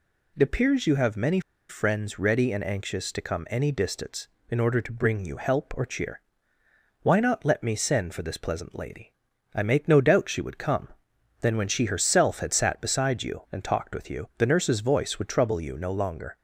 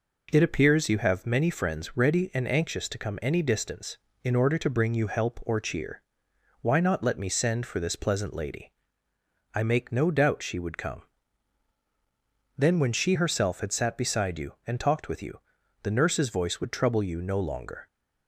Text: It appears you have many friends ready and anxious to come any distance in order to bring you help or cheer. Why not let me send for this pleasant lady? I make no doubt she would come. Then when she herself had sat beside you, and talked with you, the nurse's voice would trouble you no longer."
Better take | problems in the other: second | pauses between "many" and "friends"; slight; at 1.3 s; 0.29 s long

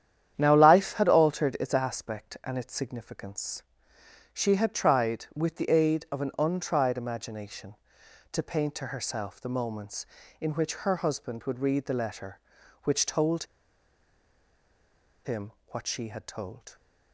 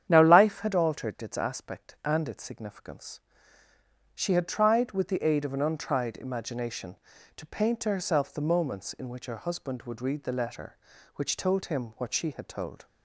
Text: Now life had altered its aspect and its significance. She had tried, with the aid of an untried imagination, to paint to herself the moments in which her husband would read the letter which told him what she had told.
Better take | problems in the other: second | starts louder than the rest; strong; until 1.3 s; 10 dB; strong in the second // pauses between "told" and "him"; strong; at 13.4 s; 1.8 s long // pauses between "him" and "what"; slight; at 15.4 s; 0.22 s long

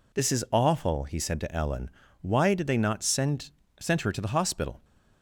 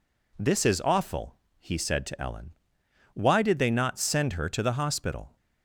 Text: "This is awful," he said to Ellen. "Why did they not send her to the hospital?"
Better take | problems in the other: second | says "send" twice; at 3.7 s

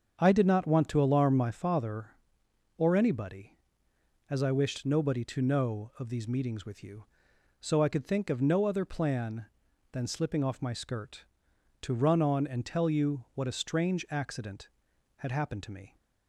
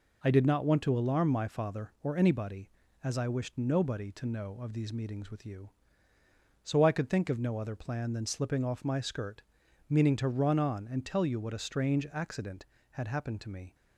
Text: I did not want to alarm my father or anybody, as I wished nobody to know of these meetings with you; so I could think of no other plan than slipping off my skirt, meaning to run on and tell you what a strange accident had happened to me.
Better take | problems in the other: second | starts louder than the rest; strong; until 1.2 s; 7 dB // skips "meaning"; at 11.5 s

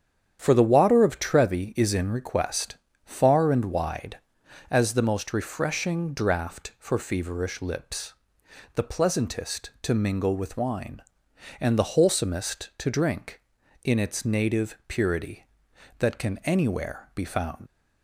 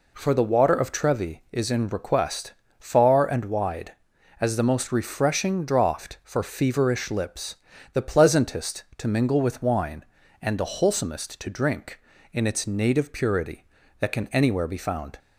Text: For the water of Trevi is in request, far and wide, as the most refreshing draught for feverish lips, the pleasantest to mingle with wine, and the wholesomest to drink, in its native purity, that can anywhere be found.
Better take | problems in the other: second | starts louder than the rest; strong; until 1.4 s; 9 dB // leaves "found" unfinished; at 17.6 s; 80 ms

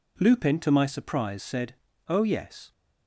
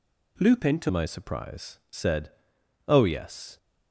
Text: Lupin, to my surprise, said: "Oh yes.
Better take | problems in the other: first | changes voice at "my"; from 0.8 s on; 2.7 s long

